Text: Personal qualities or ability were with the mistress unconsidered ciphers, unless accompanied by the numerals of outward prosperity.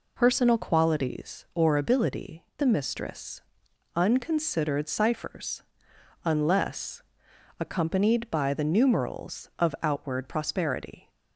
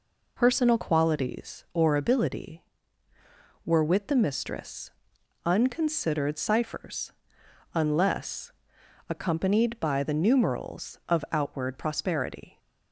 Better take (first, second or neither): second